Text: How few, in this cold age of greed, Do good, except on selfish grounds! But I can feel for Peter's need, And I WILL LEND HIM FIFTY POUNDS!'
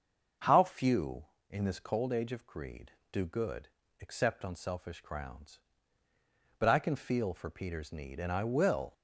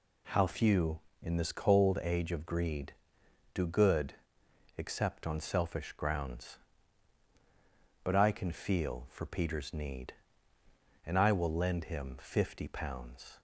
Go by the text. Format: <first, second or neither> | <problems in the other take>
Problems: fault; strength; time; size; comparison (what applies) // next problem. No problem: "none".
second | starts louder than the rest; until 1.6 s; 6.5 dB // stops before "LEND HIM FIFTY POUNDS"; at 8.9 s